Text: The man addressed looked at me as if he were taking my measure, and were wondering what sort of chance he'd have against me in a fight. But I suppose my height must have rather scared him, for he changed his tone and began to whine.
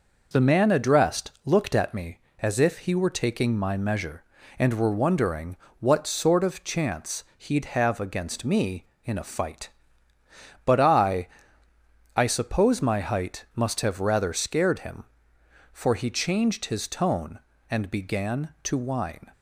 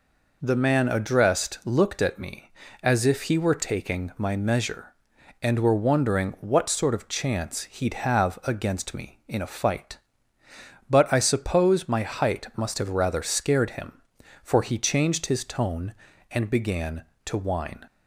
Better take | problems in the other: second | pauses between "wondering" and "what"; slight; at 5.5 s; 0.22 s long // says "I" twice; at 12.1 s

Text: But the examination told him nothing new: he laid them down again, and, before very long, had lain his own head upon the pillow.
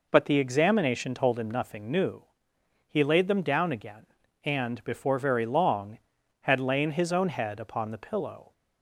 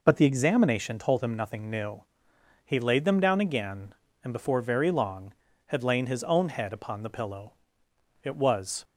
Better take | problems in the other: first | goes on to say "It was"; from 8.2 s on; 0.60 s long

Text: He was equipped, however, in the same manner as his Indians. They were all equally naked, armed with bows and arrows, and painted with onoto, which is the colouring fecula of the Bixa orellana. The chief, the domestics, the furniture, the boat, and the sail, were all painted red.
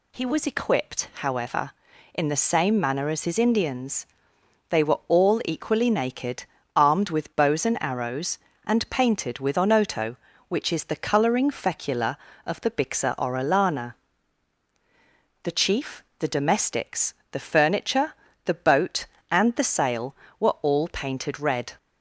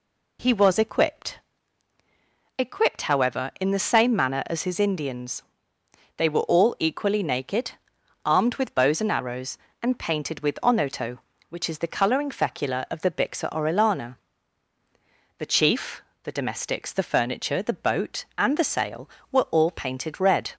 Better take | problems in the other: first | says "equipped" twice; at 2.5 s

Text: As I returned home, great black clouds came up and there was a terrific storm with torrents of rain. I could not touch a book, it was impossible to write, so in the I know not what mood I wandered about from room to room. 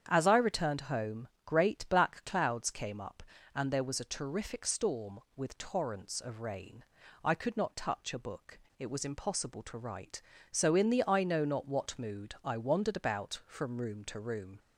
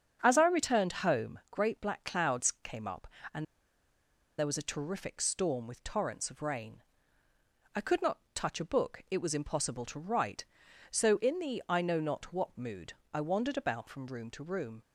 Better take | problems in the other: first | starts louder than the rest; strong; until 1.2 s; 7 dB; strong in the first // pauses between "and" and "there"; noticeable; at 3.4 s; 0.94 s long // pauses between "not" and "touch"; slight; at 8.1 s; 0.16 s long // pauses between "mood" and "I"; slight; at 12.9 s; 0.18 s long

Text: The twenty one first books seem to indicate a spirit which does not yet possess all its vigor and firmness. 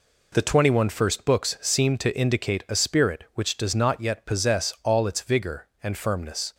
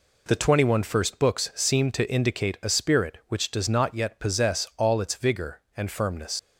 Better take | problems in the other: first | leaves "firmness" unfinished; at 6.3 s; 85 ms

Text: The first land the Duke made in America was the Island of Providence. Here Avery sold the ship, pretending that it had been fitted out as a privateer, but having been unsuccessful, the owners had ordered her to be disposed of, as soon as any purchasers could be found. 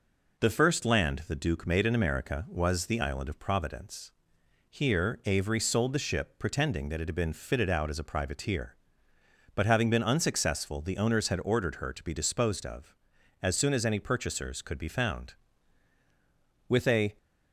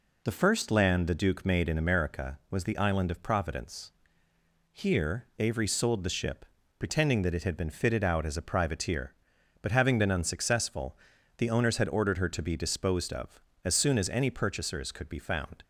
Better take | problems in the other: second | goes on to say "With a"; slight; from 16.6 s on; 0.48 s long

